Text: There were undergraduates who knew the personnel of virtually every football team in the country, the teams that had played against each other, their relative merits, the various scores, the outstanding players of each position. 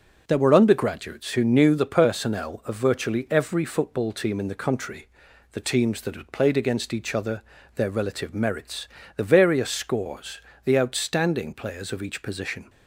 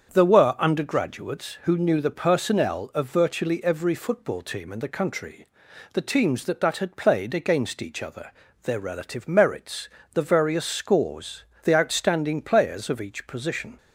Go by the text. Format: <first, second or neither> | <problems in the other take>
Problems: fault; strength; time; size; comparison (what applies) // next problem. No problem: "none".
first | starts louder than the rest; strong; until 1.1 s; 7.5 dB // says "that" twice; at 6.6 s